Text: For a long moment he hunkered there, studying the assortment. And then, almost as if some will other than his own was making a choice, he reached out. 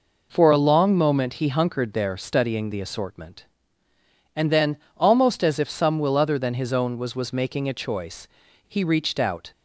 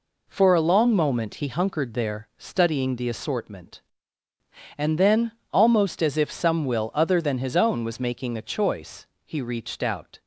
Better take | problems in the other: second | says "was" twice; at 7.1 s

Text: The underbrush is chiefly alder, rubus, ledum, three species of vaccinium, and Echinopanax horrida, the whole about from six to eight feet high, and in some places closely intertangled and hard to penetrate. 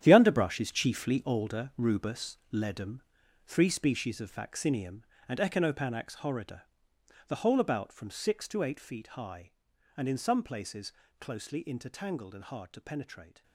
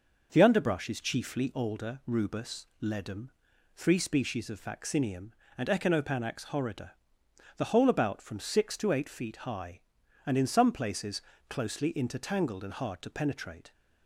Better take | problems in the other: second | gets quieter; strong; throughout; 12 dB // pauses between "places" and "closely"; slight; at 10.9 s; 0.28 s long; slight in the second

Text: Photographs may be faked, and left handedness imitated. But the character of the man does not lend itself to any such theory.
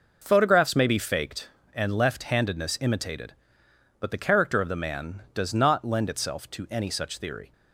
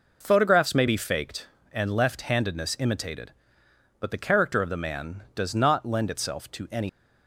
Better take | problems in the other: first | stops before "such theory"; at 6.8 s

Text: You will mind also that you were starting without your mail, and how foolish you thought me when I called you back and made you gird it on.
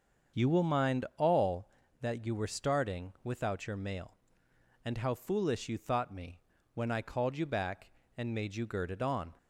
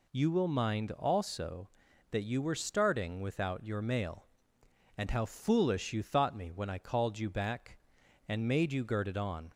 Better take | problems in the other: second | starts louder than the rest; until 1.4 s; 7 dB // says "all" for "also"; at 1.1 s // pauses between "me" and "when"; slight; at 6.3 s; 0.34 s long

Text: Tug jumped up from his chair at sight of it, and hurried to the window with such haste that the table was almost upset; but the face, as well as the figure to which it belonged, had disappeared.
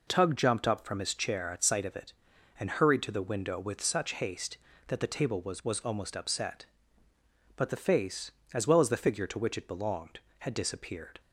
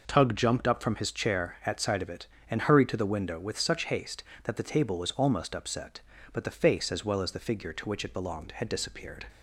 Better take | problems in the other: second | says "was" twice; at 5.6 s

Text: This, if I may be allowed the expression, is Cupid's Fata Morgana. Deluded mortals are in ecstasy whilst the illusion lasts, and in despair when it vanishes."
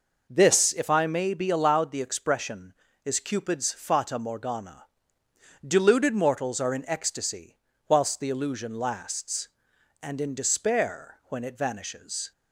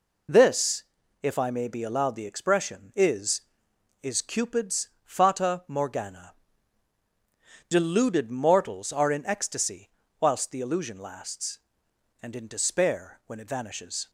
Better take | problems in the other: first | says "is" twice; at 4.0 s // pauses between "ecstasy" and "whilst"; slight; at 9.8 s; 0.30 s long; slight in the first

